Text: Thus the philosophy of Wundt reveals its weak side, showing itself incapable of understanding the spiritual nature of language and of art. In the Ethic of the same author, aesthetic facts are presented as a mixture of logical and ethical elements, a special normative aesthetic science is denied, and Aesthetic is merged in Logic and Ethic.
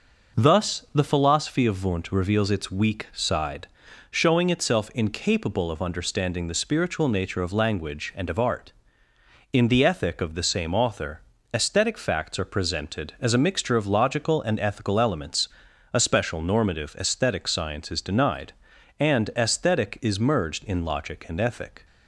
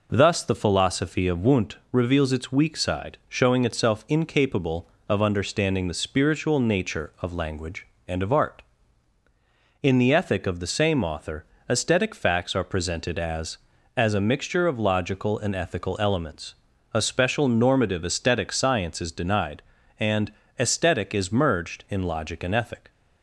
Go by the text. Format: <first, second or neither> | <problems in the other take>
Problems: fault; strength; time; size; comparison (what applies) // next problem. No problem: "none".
first | pauses between "Wundt" and "reveals"; slight; at 1.7 s; 0.16 s long // says "as" twice; at 13.9 s // pauses between "and" and "Aesthetic"; slight; at 20.3 s; 0.28 s long